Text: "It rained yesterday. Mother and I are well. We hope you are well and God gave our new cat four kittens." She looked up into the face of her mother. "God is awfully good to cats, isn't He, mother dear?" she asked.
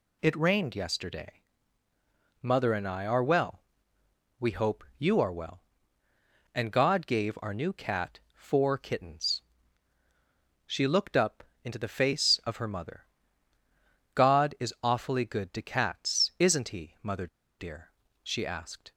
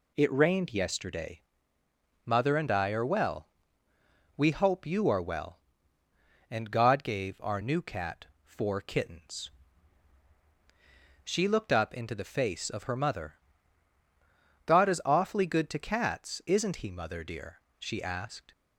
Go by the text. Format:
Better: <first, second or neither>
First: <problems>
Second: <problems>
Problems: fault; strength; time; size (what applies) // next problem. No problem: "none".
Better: second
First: pauses between "cat" and "four"; slight; at 8.1 s; 0.16 s long // pauses between "up" and "into"; slight; at 11.4 s; 0.18 s long // pauses between "mother" and "dear"; slight; at 17.2 s; 0.31 s long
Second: pauses between "cat" and "four"; slight; at 8.2 s; 0.18 s long